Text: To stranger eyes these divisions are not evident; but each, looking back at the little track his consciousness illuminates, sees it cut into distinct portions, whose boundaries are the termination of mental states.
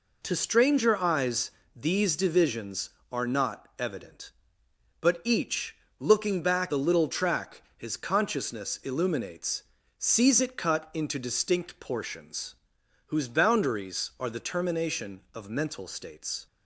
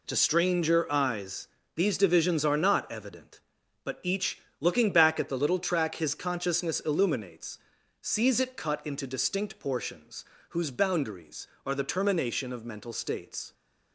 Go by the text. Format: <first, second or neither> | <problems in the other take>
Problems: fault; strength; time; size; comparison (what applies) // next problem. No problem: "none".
second | pauses between "eyes" and "these"; slight; at 1.5 s; 0.24 s long; slight in the second // skips "at"; at 6.7 s